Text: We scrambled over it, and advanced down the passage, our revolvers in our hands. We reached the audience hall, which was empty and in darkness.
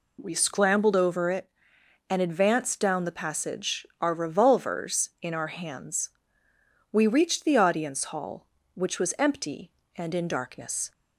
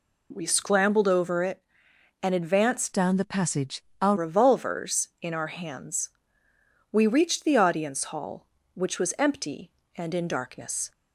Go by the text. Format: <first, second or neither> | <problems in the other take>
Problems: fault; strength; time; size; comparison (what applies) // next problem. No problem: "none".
first | changes voice from "down" to "our"; from 2.9 to 4.1 s; 1.2 s long